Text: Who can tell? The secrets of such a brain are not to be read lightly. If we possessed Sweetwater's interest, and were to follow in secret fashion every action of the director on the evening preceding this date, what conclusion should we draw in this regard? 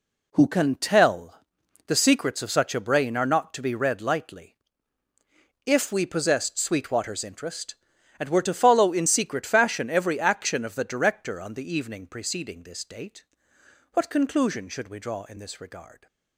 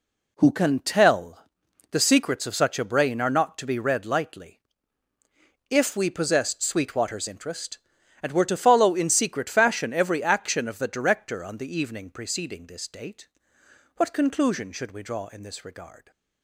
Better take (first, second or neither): neither